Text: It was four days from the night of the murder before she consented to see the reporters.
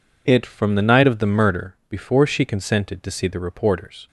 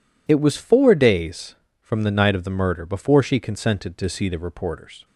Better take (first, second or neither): second